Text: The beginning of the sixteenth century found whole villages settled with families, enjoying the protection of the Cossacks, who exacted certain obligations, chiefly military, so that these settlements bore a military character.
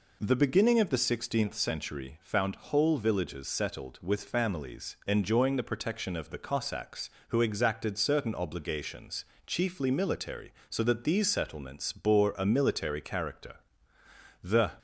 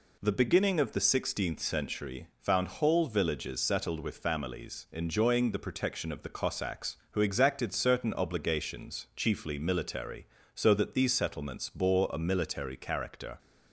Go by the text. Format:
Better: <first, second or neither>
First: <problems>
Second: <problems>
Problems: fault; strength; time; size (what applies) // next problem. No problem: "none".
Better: second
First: goes on to say "The"; slight; from 14.4 s on; 0.30 s long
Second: none